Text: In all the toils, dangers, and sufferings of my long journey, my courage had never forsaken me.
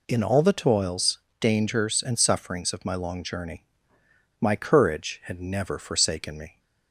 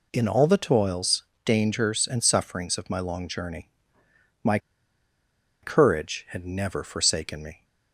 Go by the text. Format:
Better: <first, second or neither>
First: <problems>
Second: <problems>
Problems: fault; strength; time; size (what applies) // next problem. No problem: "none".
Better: first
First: none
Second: pauses between "my" and "courage"; at 4.5 s; 1.0 s long